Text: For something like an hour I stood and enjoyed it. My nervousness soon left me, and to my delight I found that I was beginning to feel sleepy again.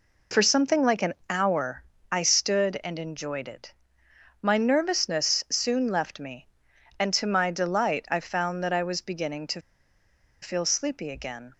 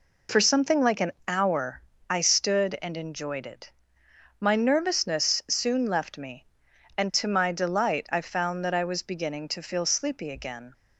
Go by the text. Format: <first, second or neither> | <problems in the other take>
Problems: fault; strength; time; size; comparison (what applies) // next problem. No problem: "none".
second | pauses between "an" and "hour"; slight; at 1.1 s; 0.16 s long; slight in the second // pauses between "hour" and "I"; slight; at 1.8 s; 0.26 s long; slight in the second // pauses between "to" and "feel"; noticeable; at 9.5 s; 0.81 s long